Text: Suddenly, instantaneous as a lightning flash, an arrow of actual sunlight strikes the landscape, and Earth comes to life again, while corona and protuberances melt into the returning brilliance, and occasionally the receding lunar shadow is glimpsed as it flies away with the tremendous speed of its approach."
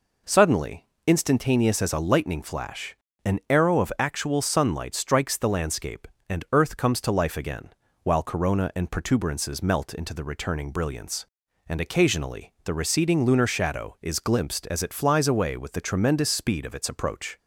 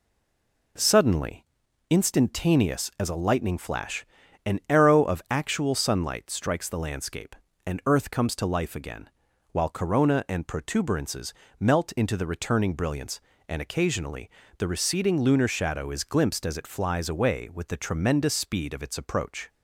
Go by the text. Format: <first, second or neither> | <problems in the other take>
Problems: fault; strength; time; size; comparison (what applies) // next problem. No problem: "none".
first | stays silent before the first word; slight; until 0.7 s; 0.7 s long // pauses between "protuberances" and "melt"; slight; at 11.3 s; 0.26 s long // pauses between "occasionally" and "the"; slight; at 14.2 s; 0.30 s long